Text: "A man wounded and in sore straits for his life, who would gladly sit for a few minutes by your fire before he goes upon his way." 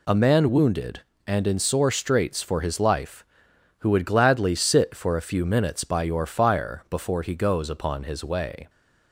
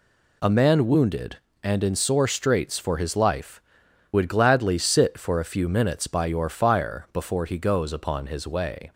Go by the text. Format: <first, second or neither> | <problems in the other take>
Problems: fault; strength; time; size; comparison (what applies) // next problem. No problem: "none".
first | skips "who"; at 3.8 s